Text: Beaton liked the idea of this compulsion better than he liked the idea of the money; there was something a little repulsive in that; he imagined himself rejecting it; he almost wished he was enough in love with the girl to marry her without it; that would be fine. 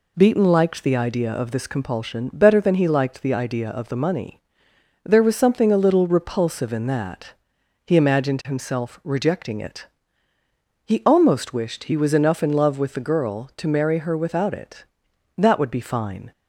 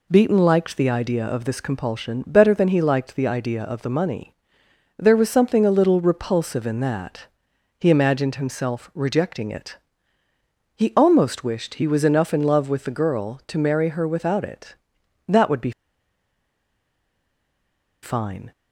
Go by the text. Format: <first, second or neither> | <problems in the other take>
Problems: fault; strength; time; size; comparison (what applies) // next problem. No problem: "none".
first | pauses between "be" and "fine"; strong; at 15.7 s; 2.3 s long